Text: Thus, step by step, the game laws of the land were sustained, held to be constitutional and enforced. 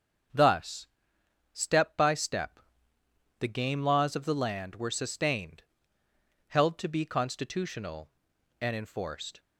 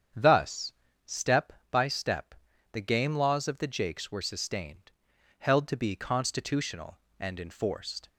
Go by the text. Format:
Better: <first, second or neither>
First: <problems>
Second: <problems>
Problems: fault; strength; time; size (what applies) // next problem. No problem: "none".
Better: first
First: starts louder than the rest; until 1.9 s; 7 dB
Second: starts louder than the rest; strong; until 1.4 s; 8 dB // says "jakes" for "land"; at 3.6 s